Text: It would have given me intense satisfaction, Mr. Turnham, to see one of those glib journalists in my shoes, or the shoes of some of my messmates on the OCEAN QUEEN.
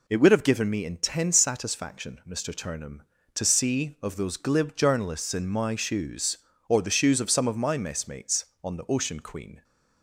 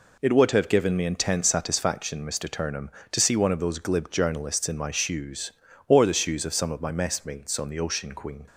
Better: second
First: skips "one"; at 3.9 s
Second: none

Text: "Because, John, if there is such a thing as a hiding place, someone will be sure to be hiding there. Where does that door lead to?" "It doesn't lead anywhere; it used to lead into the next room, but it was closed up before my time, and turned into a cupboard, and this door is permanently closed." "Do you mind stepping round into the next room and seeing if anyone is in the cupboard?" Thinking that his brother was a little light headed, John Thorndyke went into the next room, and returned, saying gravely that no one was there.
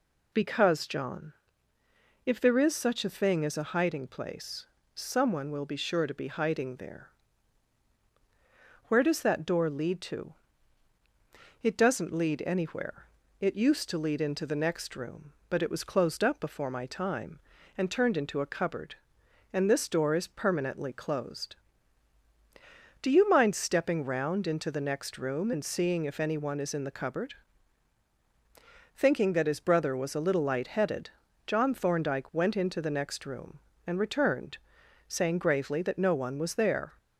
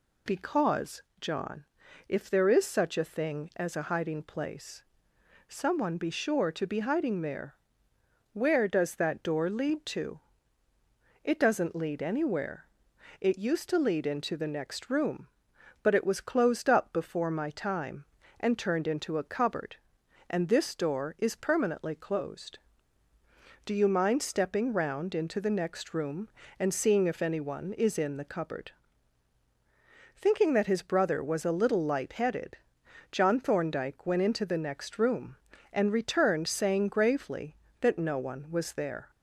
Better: first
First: none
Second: skips "will"; at 5.9 s

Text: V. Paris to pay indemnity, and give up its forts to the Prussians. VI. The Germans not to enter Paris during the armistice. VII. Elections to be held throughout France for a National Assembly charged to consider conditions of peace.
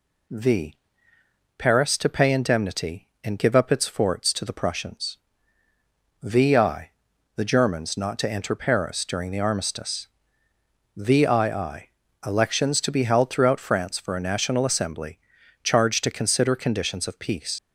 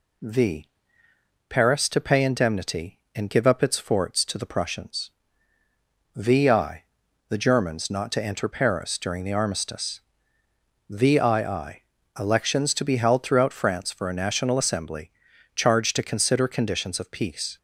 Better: second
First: pauses between "Assembly" and "charged"; at 15.1 s; 0.42 s long // leaves "peace" unfinished; at 17.5 s; 65 ms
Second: pauses between "Assembly" and "charged"; at 15.1 s; 0.42 s long

